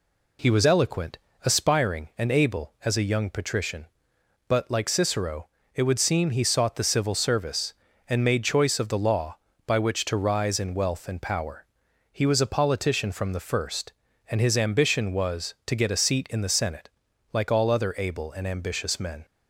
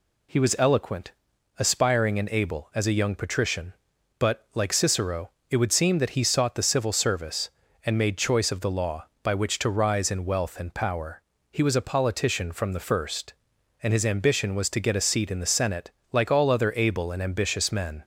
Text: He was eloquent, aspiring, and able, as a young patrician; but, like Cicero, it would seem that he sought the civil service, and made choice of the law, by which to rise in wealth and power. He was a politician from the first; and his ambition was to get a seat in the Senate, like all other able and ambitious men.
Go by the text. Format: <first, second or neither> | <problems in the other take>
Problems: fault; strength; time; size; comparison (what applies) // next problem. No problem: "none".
second | skips "that"; at 6.3 s